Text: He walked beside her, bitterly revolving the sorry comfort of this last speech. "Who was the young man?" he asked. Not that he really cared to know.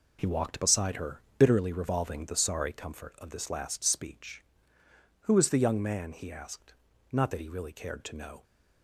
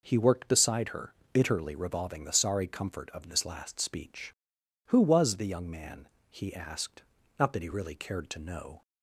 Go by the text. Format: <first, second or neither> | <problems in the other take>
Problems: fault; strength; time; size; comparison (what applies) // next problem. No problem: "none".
first | says "worked" for "walked"; at 0.1 s